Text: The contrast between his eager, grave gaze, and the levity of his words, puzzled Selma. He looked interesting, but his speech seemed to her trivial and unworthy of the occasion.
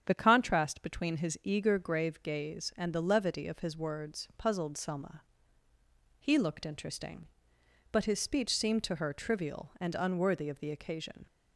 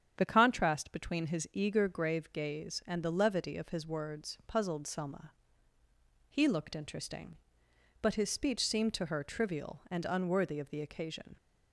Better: neither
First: starts louder than the rest; strong; until 1.0 s; 8 dB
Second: starts louder than the rest; strong; until 1.1 s; 8.5 dB

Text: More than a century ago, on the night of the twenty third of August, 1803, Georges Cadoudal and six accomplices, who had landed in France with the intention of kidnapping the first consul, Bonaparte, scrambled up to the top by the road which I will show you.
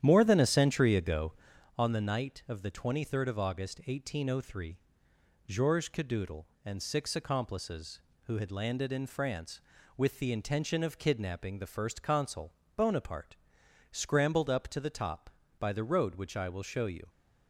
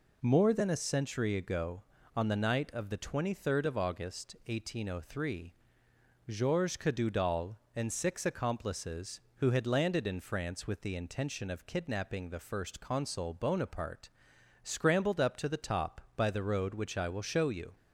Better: second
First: starts louder than the rest; strong; until 1.6 s; 10 dB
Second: none

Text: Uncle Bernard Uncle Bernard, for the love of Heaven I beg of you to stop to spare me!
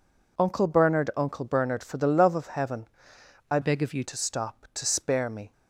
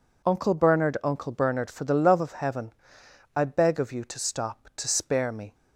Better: second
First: pauses between "Heaven" and "I"; noticeable; at 2.8 s; 0.64 s long // changes voice from "beg" to "you"; from 3.6 to 4.0 s; 0.4 s long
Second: pauses between "Heaven" and "I"; noticeable; at 2.7 s; 0.64 s long

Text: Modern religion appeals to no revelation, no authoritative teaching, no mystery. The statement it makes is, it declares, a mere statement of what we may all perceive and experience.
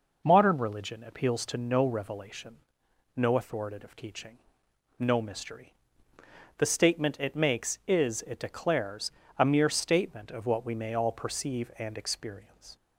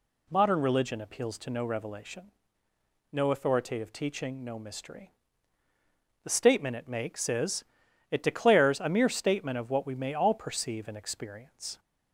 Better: neither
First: none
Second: none

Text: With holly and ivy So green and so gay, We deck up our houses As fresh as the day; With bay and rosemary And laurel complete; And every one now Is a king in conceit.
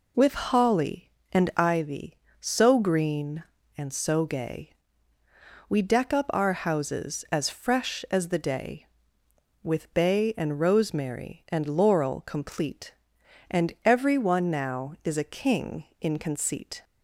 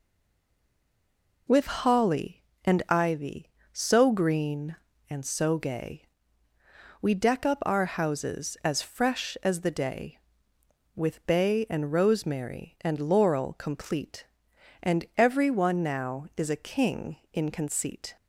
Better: first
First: none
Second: stays silent before the first word; noticeable; until 1.4 s; 1.4 s long

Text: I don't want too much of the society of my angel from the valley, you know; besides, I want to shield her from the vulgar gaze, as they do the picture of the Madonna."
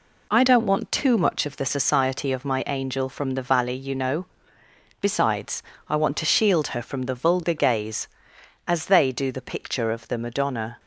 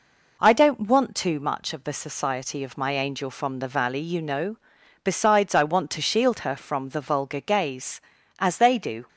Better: first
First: none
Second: stops before "the picture of the Madonna"; at 9.0 s

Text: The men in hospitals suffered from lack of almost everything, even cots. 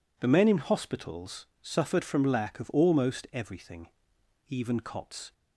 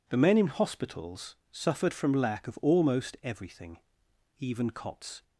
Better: neither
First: pauses between "hospitals" and "suffered"; slight; at 1.4 s; 0.16 s long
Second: pauses between "hospitals" and "suffered"; slight; at 1.3 s; 0.16 s long

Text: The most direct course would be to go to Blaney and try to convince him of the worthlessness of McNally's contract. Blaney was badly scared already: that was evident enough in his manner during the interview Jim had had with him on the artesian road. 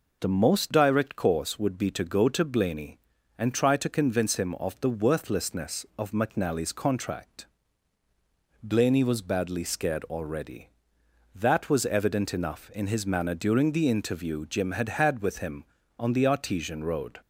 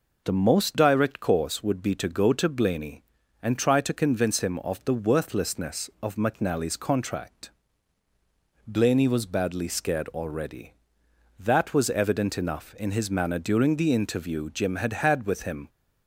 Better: first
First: none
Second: stops before "on the artesian road"; at 15.6 s

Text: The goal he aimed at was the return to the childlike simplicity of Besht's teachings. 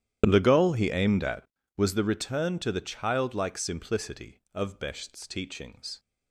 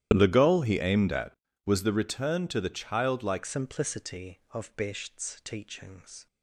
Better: first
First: starts louder than the rest; strong; until 1.2 s; 11 dB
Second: starts louder than the rest; strong; until 1.1 s; 12 dB // changes voice at "simplicity"; from 3.4 s on; 2.8 s long

